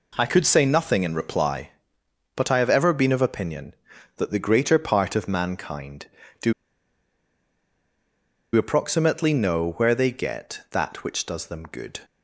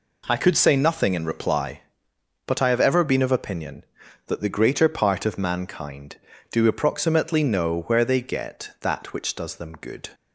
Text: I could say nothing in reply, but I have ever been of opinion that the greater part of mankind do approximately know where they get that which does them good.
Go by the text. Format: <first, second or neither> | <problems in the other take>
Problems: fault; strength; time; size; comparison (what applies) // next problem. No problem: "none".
second | pauses between "do" and "approximately"; strong; at 6.5 s; 2.0 s long